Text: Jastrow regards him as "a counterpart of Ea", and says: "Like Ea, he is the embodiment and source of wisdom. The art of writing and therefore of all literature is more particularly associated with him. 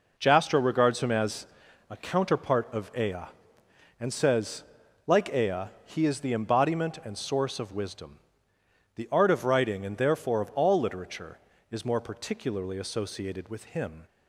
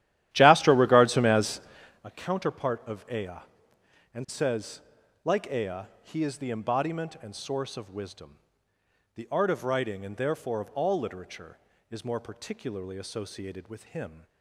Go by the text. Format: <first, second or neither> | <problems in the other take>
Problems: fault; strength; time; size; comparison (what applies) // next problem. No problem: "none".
first | starts louder than the rest; strong; until 2.1 s; 13 dB // pauses between "as" and "a"; at 1.5 s; 0.44 s long; also in the first